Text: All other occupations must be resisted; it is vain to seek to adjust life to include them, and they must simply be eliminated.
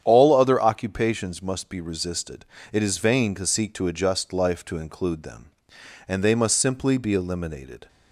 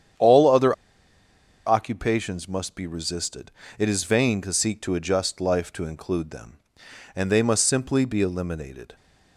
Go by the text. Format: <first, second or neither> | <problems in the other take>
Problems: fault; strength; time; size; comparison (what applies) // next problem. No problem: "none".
first | starts louder than the rest; strong; until 2.1 s; 9 dB; strong in the first // pauses between "other" and "occupations"; noticeable; at 0.7 s; 0.92 s long